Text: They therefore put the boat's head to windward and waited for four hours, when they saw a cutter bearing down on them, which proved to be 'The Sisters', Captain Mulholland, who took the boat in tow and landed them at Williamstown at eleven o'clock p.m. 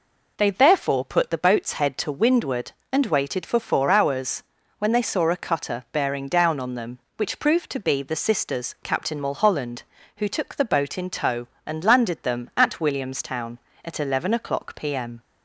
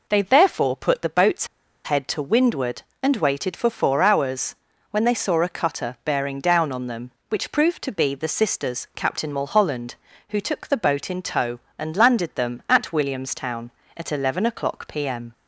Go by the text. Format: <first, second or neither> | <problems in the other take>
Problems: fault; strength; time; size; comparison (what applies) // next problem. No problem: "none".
first | pauses between "boat's" and "head"; at 1.4 s; 0.37 s long